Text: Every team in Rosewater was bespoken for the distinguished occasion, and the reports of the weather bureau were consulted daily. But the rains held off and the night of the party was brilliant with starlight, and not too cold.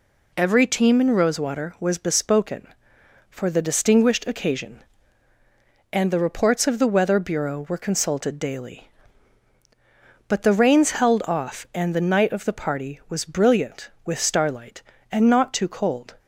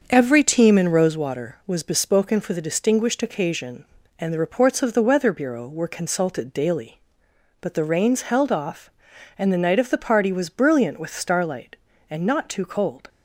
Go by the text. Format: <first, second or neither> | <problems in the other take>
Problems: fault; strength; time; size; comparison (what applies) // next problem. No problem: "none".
first | starts louder than the rest; until 1.2 s; 6.5 dB